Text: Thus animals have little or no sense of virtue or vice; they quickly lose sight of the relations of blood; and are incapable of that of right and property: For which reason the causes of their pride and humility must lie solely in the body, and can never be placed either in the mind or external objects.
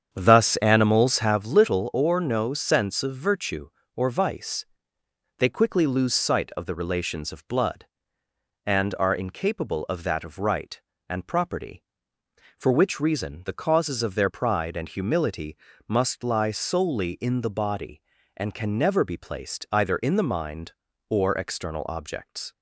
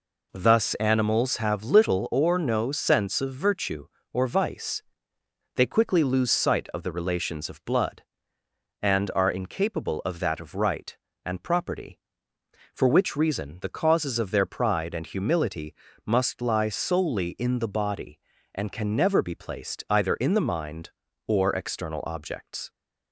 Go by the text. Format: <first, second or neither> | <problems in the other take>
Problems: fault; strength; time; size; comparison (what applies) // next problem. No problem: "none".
second | starts louder than the rest; strong; until 1.5 s; 8 dB // pauses between "humility" and "must"; slight; at 15.5 s; 0.30 s long; slight in the second